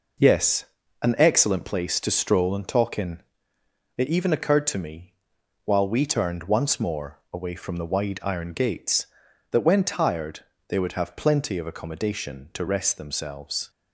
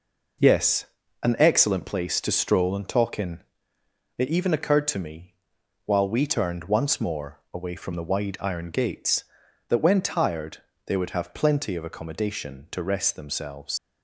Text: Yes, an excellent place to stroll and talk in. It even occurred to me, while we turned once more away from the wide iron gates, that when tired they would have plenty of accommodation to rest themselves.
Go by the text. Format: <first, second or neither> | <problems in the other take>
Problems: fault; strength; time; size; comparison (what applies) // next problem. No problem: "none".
first | pauses between "tired" and "they"; slight; at 10.5 s; 0.28 s long; slight in the first // leaves "themselves" unfinished; at 13.7 s; 110 ms